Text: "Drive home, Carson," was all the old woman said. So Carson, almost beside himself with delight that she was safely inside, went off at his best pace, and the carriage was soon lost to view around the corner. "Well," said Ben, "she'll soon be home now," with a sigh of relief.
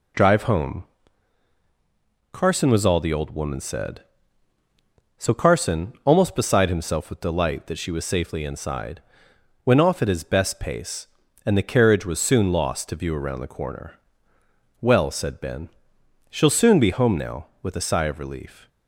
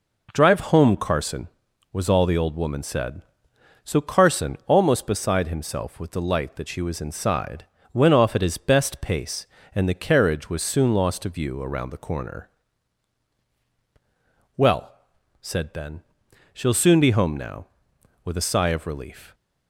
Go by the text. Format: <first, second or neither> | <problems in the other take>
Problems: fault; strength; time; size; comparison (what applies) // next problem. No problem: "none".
first | skips "safely"; at 7.0 s